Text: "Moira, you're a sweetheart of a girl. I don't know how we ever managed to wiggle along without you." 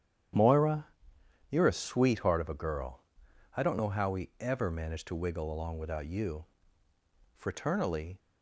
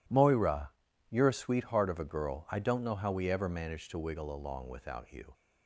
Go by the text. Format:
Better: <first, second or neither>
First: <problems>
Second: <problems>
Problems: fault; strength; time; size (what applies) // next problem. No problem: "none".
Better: second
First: starts louder than the rest; strong; until 1.9 s; 10 dB // goes on to say "Fraternally"; noticeable; from 7.3 s on; 0.82 s long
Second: none